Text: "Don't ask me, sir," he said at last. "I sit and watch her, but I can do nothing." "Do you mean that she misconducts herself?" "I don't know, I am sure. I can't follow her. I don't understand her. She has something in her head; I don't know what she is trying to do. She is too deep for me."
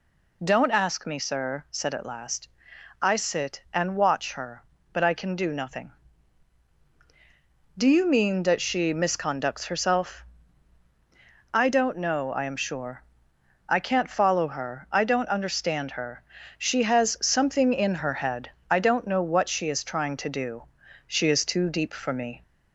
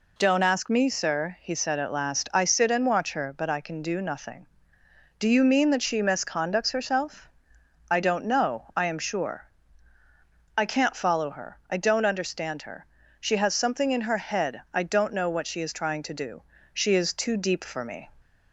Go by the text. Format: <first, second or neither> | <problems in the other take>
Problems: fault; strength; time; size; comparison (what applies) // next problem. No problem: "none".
second | skips "he"; at 1.6 s